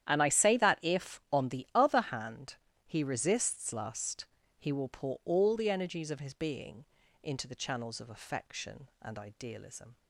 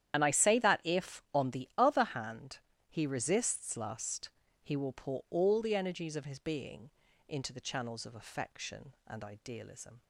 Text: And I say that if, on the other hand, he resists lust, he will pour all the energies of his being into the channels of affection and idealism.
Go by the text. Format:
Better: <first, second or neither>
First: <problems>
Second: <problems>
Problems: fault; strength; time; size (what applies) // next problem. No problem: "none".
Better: first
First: starts louder than the rest; strong; until 1.1 s; 10.5 dB // pauses between "being" and "into"; at 6.8 s; 0.38 s long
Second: loses the start of "And"; at 0.1 s; 60 ms // starts louder than the rest; strong; until 1.1 s; 10.5 dB // pauses between "being" and "into"; at 6.9 s; 0.38 s long